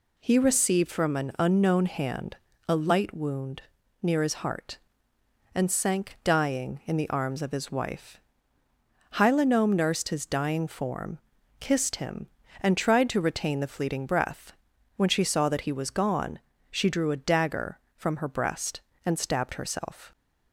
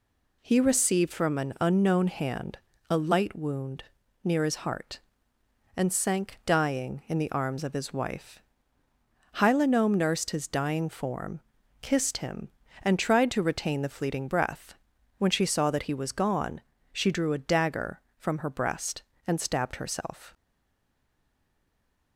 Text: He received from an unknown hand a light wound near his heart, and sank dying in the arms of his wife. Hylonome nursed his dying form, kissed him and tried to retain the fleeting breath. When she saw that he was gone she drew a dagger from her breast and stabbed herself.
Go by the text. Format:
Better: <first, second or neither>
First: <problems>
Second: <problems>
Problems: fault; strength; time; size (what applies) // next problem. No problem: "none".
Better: first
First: pauses between "hand" and "a"; slight; at 2.3 s; 0.30 s long // pauses between "wound" and "near"; at 3.6 s; 0.40 s long // pauses between "gone" and "she"; slight; at 16.3 s; 0.32 s long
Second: pauses between "hand" and "a"; slight; at 2.5 s; 0.30 s long // pauses between "wound" and "near"; at 3.8 s; 0.40 s long // pauses between "gone" and "she"; slight; at 16.6 s; 0.32 s long // stays silent after the last word; noticeable; from 20.3 s on; 1.8 s long